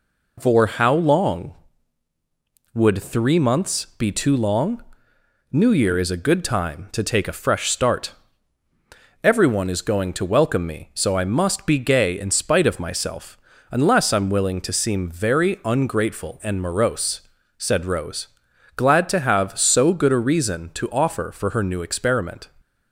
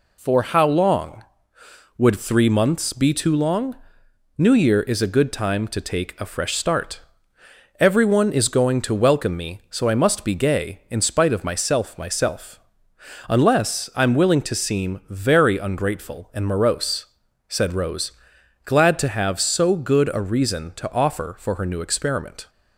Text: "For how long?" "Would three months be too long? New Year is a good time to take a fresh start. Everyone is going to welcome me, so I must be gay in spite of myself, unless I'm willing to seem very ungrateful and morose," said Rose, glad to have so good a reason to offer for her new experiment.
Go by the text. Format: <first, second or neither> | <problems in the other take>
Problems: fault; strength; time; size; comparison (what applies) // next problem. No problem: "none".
first | says "myself" twice; at 11.9 s